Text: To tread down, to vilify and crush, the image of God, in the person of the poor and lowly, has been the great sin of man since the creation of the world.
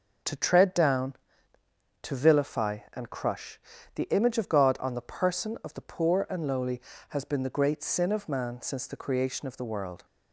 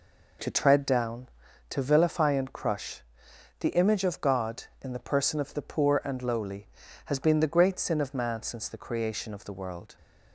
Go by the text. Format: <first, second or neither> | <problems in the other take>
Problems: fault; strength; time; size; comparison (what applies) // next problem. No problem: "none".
second | starts louder than the rest; until 2.1 s; 6 dB // says "on" for "in"; at 4.7 s